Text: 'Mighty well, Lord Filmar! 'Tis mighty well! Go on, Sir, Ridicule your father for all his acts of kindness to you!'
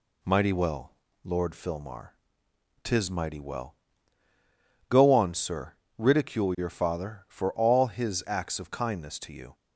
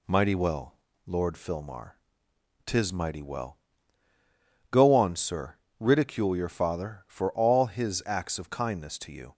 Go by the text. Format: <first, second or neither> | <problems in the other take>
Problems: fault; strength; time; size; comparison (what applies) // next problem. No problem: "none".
neither | none